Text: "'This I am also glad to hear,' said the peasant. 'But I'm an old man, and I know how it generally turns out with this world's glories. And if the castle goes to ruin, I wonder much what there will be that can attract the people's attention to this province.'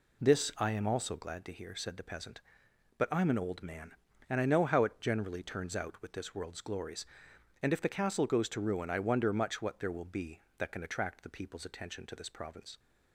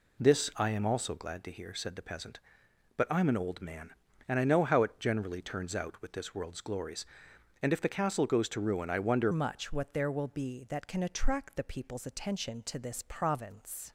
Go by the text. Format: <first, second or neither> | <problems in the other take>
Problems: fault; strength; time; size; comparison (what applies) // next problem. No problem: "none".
first | changes voice at "much"; from 9.2 s on; 4.7 s long